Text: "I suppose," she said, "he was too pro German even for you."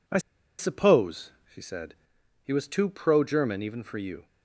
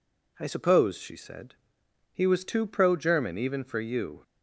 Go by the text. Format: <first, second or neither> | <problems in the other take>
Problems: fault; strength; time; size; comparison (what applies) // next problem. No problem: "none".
second | pauses between "I" and "suppose"; at 0.1 s; 0.40 s long